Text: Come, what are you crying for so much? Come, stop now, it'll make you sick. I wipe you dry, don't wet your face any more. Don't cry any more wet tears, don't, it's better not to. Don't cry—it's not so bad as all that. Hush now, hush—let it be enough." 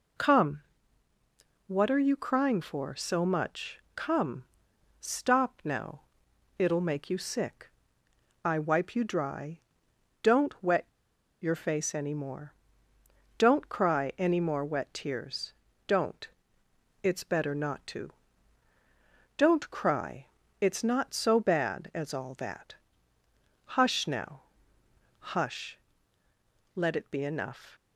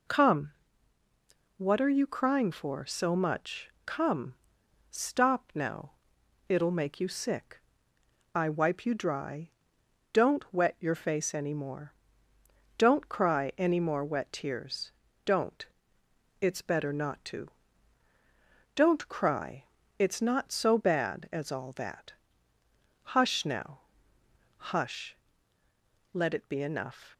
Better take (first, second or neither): second